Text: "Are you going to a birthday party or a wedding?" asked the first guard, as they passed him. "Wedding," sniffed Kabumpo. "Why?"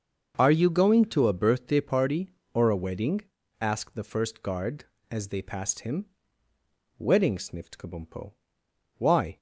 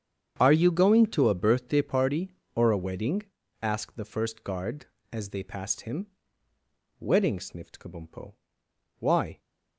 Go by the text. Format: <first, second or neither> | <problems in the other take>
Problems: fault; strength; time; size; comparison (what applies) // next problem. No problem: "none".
first | gets quieter; strong; throughout; 15.5 dB // starts louder than the rest; strong; until 1.3 s; 8 dB; also in the first